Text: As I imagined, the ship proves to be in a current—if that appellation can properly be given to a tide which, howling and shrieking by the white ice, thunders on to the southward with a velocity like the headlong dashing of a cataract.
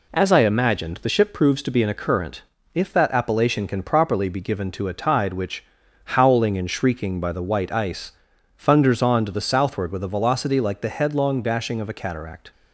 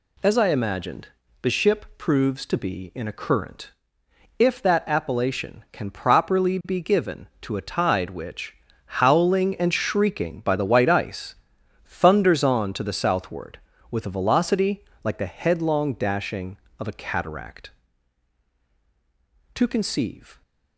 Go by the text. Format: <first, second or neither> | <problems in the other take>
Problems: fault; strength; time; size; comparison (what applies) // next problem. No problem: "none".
first | pauses between "velocity" and "like"; slight; at 14.8 s; 0.20 s long // goes on to say "To conceive"; noticeable; from 19.5 s on; 0.86 s long